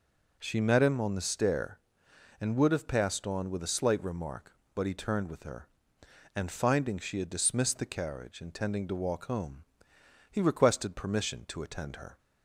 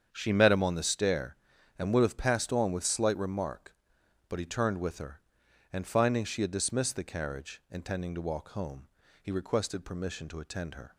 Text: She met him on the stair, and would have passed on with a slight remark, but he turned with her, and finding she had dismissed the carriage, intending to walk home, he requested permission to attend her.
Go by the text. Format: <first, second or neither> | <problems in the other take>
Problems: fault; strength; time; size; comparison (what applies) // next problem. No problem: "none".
first | starts louder than the rest; strong; until 1.1 s; 8 dB // skips "a"; at 2.8 s